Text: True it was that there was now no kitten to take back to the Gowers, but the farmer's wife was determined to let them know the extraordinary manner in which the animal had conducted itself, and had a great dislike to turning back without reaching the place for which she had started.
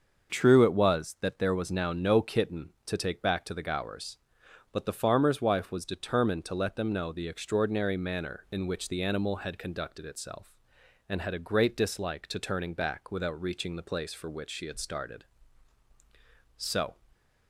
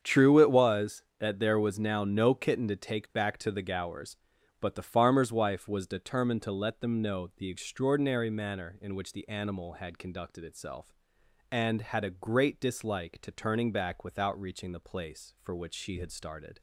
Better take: second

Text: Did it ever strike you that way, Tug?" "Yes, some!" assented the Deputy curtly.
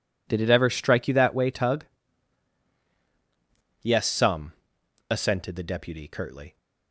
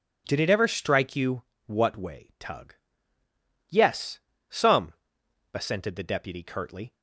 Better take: first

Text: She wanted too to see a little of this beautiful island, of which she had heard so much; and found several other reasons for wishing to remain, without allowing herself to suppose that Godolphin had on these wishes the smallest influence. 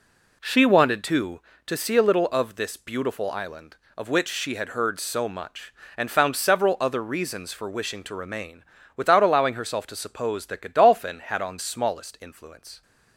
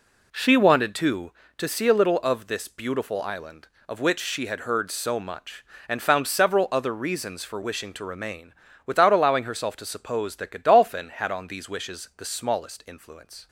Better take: second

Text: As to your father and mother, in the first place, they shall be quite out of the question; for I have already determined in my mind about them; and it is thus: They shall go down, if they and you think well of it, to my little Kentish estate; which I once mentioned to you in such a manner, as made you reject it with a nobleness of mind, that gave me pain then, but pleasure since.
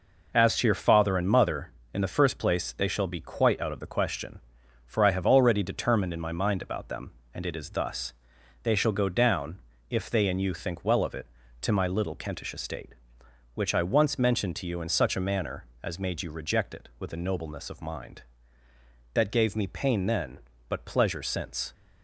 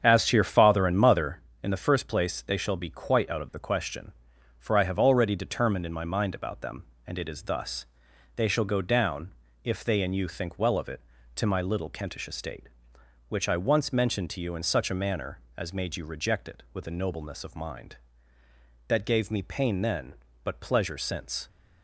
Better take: first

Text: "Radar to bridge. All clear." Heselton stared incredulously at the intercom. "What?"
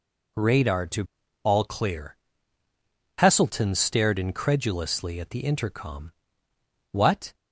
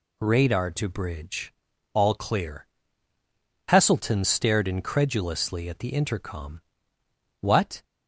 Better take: second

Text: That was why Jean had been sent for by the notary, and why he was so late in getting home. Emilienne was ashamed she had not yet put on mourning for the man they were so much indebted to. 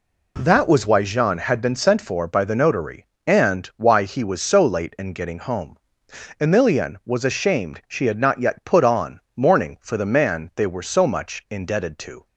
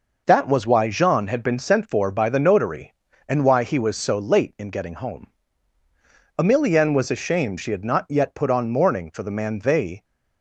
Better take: first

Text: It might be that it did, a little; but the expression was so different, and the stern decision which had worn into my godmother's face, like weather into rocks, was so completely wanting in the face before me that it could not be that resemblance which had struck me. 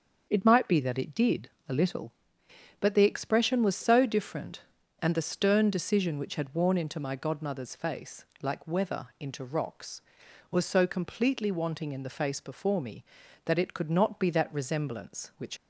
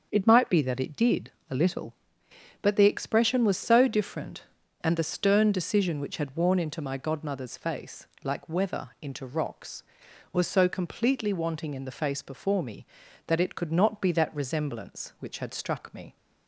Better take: second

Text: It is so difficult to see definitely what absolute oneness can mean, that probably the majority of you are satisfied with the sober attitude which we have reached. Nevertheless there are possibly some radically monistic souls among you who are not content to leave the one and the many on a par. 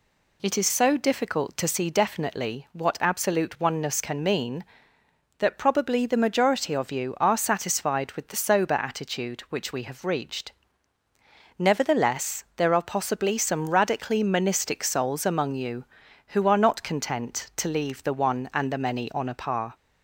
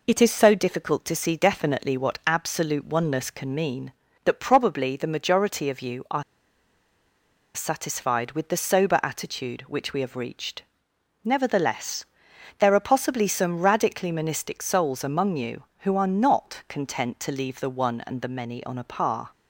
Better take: first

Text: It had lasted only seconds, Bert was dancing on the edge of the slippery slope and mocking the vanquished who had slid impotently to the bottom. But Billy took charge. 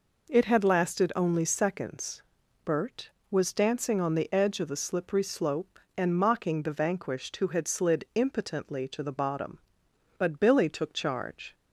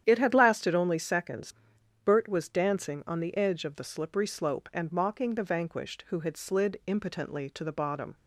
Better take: first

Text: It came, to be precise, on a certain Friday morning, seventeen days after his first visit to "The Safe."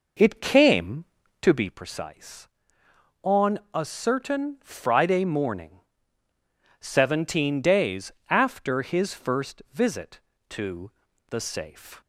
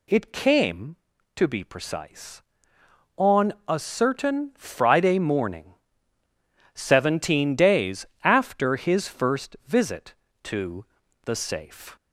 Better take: second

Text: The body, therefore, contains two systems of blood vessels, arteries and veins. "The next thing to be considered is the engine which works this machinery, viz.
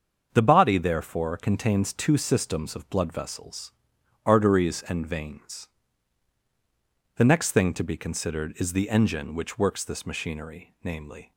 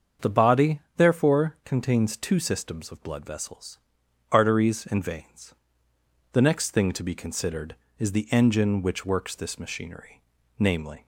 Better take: neither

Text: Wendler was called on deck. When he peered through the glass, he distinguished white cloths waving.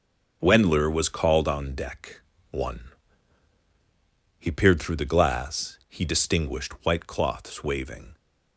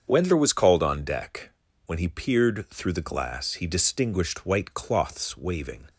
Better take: second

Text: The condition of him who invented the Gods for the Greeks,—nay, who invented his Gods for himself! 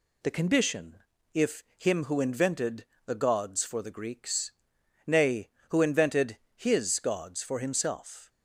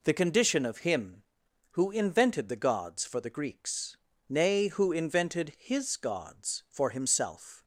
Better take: second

